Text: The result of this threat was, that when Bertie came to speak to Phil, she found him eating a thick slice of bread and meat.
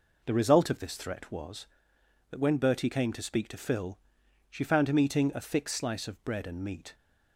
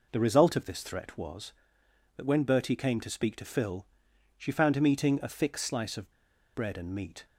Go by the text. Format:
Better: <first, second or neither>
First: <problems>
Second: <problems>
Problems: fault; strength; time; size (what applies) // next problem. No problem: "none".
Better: first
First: none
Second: pauses between "of" and "bread"; at 6.1 s; 0.43 s long